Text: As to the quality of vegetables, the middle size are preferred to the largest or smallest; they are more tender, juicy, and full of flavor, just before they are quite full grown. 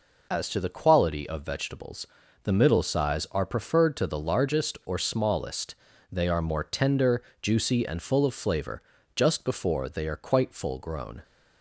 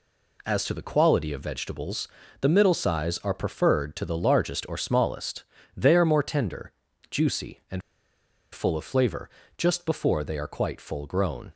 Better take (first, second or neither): first